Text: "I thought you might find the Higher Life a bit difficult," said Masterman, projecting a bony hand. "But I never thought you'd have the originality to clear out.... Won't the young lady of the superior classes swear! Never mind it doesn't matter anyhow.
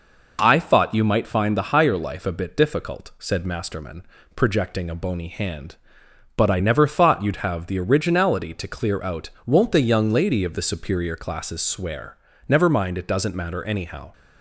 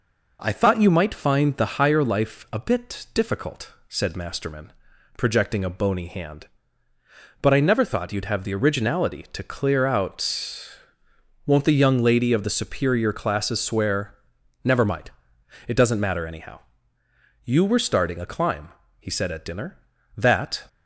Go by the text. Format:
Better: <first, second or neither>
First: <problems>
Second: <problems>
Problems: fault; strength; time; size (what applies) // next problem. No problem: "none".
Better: first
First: none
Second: pauses between "mind" and "it"; noticeable; at 15.0 s; 0.56 s long // goes on to say "You were starting a climb he said at dinner that"; strong; from 17.4 s on; 3.2 s long